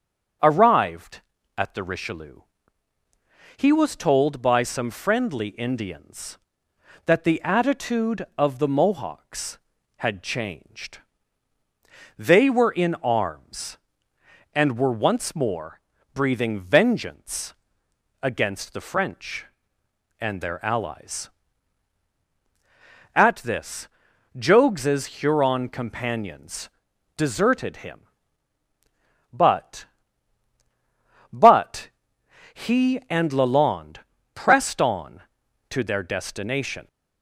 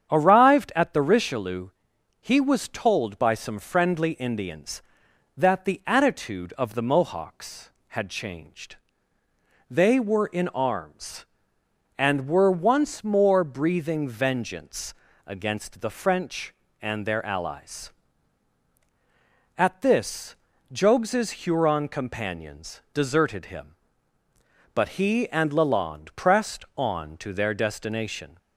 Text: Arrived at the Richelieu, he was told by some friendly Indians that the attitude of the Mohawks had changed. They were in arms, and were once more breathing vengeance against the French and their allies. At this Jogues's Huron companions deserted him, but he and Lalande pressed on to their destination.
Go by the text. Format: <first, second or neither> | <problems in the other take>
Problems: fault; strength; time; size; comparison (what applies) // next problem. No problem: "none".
second | starts louder than the rest; strong; until 1.7 s; 7 dB; strong in the second // pauses between "more" and "breathing"; slight; at 15.8 s; 0.34 s long // pauses between "vengeance" and "against"; noticeable; at 17.5 s; 0.70 s long; slight in the second // pauses between "this" and "Jogues's"; noticeable; at 23.8 s; 0.48 s long; slight in the second // pauses between "companions" and "deserted"; noticeable; at 26.6 s; 0.48 s long // says "but" twice; at 31.3 s // pauses between "Lalande" and "pressed"; slight; at 33.9 s; 0.34 s long